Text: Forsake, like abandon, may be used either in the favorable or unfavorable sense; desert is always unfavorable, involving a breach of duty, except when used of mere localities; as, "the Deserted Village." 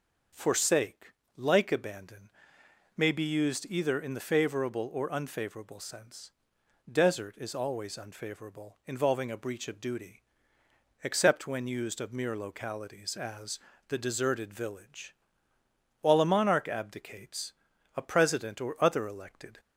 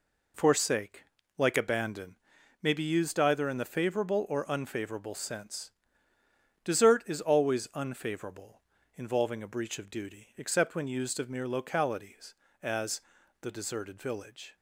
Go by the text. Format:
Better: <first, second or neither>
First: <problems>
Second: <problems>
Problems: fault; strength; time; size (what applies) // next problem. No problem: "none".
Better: second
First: goes on to say "While a monarch abdicates a president or other elected"; strong; from 16.0 s on; 3.5 s long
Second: none